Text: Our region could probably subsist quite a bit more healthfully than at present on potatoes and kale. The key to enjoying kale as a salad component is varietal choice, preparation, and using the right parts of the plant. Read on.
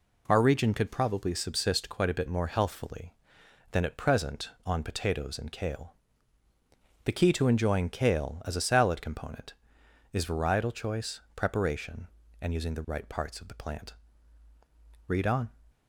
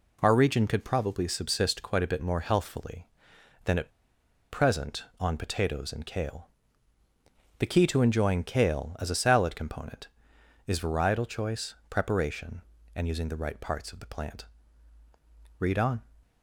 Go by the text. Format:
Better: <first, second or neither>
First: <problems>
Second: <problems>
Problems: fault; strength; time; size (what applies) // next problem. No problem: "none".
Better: first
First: none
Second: pauses between "at" and "present"; noticeable; at 3.8 s; 0.62 s long